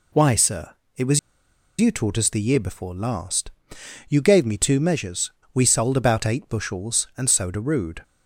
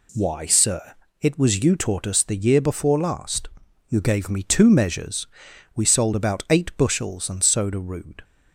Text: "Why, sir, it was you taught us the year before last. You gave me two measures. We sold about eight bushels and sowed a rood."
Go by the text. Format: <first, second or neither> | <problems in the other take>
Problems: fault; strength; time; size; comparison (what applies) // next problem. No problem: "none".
second | pauses between "was" and "you"; noticeable; at 1.1 s; 0.61 s long